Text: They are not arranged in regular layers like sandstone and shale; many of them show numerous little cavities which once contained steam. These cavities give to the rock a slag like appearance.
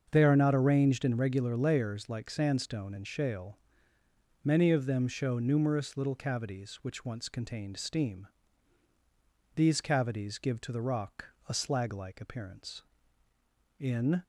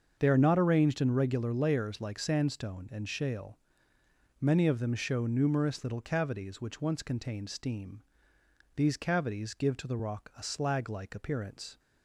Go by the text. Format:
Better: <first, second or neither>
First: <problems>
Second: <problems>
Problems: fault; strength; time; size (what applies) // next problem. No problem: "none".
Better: second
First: starts louder than the rest; until 1.1 s; 6.5 dB // pauses between "rock" and "a"; slight; at 11.2 s; 0.24 s long // goes on to say "In"; slight; from 13.8 s on; 0.42 s long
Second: starts louder than the rest; until 1.1 s; 6.5 dB